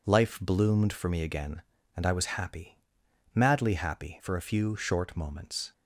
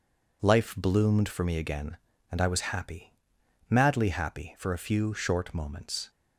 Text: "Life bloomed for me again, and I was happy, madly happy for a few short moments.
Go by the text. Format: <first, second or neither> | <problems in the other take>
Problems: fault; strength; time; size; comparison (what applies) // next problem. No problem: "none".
neither | none